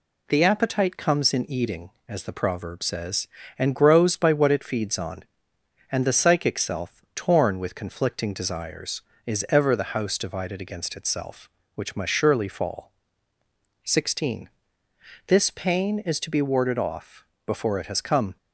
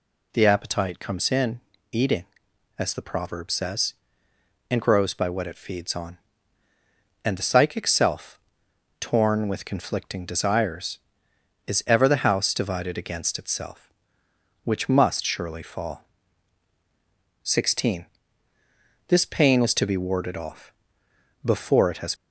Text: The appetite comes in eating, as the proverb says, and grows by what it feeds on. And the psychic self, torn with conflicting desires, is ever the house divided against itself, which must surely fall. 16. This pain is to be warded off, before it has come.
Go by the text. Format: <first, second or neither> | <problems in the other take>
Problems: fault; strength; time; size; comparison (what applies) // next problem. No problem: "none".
first | pauses between "in" and "eating"; slight; at 1.6 s; 0.32 s long // stops before "come"; at 22.1 s